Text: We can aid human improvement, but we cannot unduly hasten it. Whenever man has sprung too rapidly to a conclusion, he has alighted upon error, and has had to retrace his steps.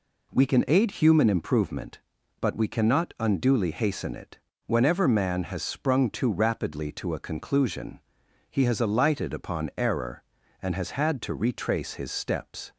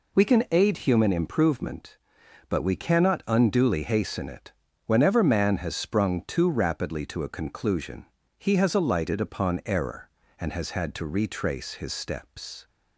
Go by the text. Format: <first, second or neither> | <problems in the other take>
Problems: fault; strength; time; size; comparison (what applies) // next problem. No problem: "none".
neither | none